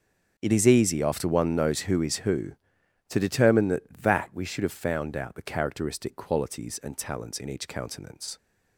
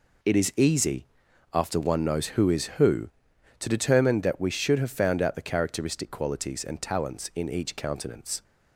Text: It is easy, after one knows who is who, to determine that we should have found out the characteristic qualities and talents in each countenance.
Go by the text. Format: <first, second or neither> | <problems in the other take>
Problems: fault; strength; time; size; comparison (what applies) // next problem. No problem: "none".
second | starts louder than the rest; noticeable; until 1.3 s; 6 dB // says "that" twice; at 4.0 s